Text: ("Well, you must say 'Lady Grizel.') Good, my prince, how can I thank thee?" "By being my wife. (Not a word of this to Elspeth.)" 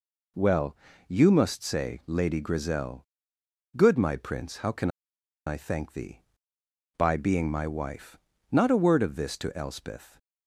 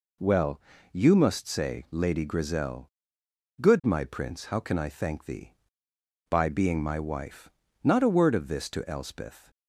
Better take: second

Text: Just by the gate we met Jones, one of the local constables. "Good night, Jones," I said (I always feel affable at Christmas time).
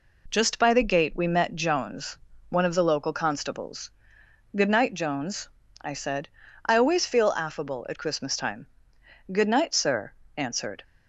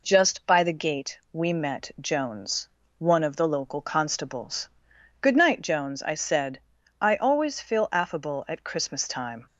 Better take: second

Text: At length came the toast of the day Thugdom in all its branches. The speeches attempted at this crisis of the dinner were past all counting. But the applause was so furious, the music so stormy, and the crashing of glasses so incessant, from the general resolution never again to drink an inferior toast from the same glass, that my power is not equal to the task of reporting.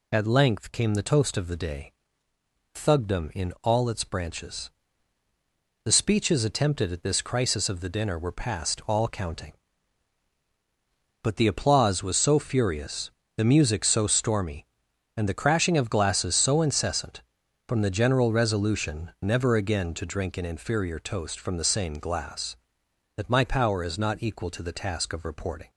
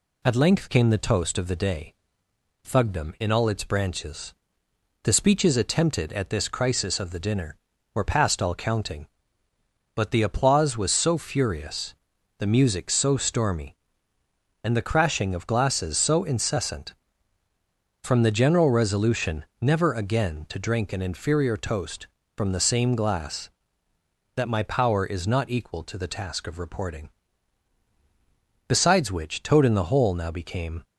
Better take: first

